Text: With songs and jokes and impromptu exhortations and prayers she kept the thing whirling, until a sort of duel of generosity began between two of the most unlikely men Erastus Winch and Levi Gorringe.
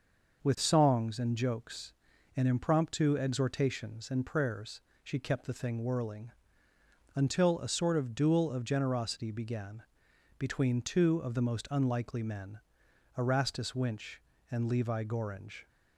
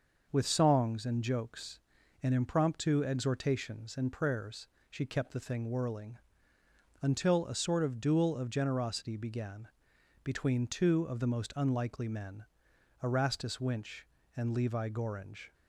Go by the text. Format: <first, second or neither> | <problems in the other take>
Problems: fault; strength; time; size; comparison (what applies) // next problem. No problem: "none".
neither | pauses between "prayers" and "she"; slight; the same in both // pauses between "began" and "between"; noticeable; the same in both // pauses between "men" and "Erastus"; noticeable; the same in both